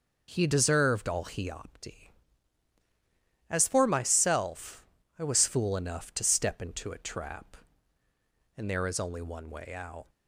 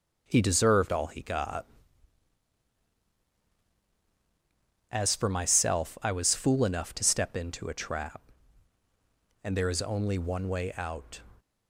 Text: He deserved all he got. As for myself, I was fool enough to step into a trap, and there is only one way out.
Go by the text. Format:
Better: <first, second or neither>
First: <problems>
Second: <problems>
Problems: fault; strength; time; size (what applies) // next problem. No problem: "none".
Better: second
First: says "opti" for "got"; at 1.4 s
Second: none